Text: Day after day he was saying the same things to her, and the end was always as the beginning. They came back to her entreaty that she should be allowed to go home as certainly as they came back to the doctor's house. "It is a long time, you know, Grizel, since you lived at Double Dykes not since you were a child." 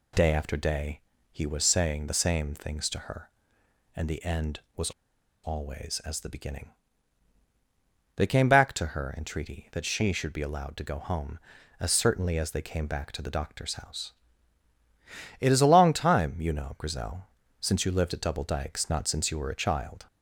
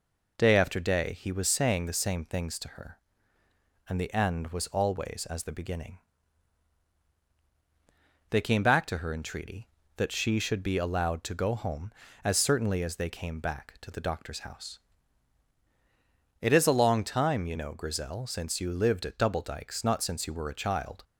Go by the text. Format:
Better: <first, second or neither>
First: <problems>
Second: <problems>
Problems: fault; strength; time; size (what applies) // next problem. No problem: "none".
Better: second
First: pauses between "day" and "he"; slight; at 1.0 s; 0.32 s long // pauses between "was" and "always"; noticeable; at 4.9 s; 0.53 s long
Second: none